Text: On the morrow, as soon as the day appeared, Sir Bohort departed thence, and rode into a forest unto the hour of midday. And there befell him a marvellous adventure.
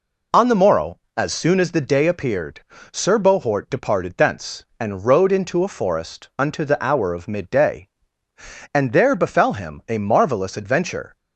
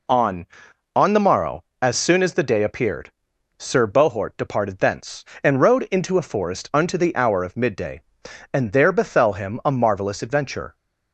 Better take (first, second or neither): first